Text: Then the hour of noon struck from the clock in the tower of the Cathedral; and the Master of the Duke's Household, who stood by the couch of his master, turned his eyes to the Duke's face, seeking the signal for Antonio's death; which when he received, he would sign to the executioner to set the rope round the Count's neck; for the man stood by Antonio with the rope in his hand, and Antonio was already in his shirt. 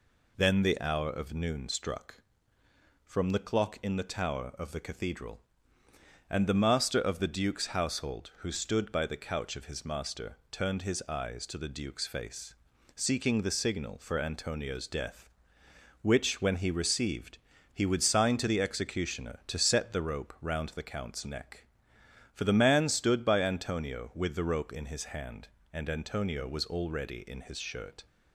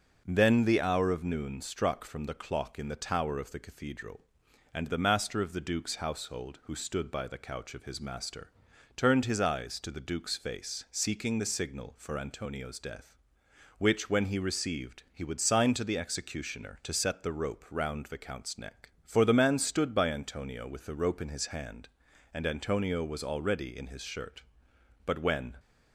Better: first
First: none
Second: starts louder than the rest; until 1.2 s; 6 dB // goes on to say "But when"; from 25.0 s on; 0.52 s long

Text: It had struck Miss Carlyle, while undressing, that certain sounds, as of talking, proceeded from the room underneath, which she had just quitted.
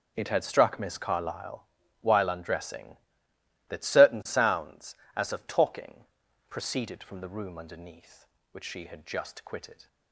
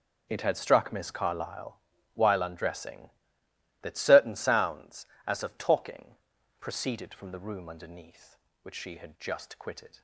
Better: neither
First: none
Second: none

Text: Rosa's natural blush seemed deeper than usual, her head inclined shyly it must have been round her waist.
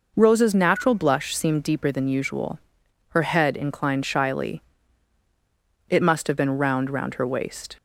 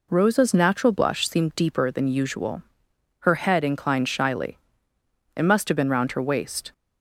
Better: second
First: pauses between "shyly" and "it"; strong; at 4.6 s; 1.2 s long // says "round" twice; at 6.9 s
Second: pauses between "shyly" and "it"; noticeable; at 4.5 s; 0.80 s long

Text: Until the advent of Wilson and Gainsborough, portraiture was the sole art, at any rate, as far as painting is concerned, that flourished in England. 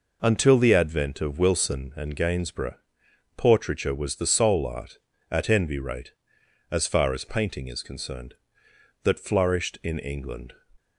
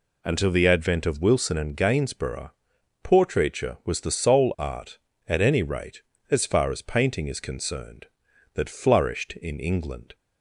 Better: second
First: says "envy" for "any"; at 5.4 s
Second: none

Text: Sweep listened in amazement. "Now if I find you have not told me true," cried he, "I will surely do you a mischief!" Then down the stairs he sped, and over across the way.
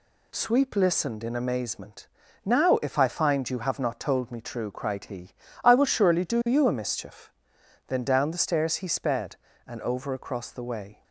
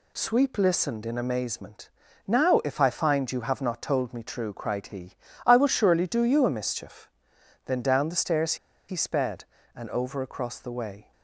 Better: first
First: none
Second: pauses between "stairs" and "he"; slight; at 8.5 s; 0.33 s long

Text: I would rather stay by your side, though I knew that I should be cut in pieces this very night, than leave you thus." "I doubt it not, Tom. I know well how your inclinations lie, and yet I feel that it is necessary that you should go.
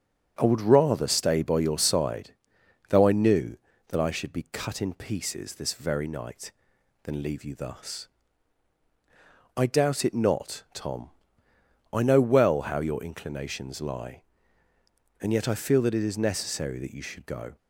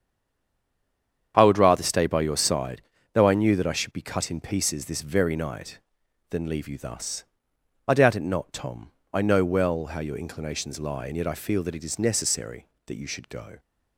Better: first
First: starts louder than the rest; until 1.3 s; 6.5 dB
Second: stays silent before the first word; noticeable; until 1.3 s; 1.3 s long // starts louder than the rest; strong; until 2.3 s; 8 dB

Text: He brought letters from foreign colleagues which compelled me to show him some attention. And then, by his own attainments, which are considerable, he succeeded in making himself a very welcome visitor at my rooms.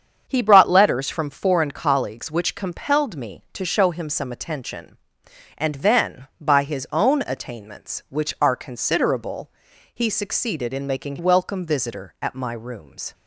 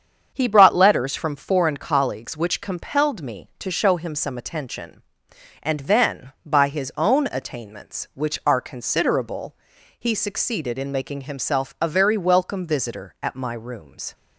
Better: second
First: starts louder than the rest; strong; until 1.2 s; 7.5 dB // skips "himself a very"; at 11.1 s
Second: starts louder than the rest; strong; until 1.3 s; 7.5 dB

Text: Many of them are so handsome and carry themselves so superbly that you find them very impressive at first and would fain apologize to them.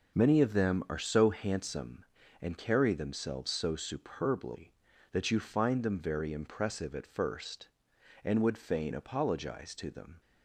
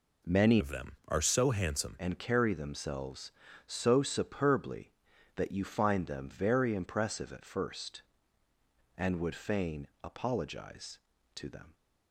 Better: first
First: none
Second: changes voice from "of" to "handsome"; from 0.5 to 1.9 s; 1.4 s long

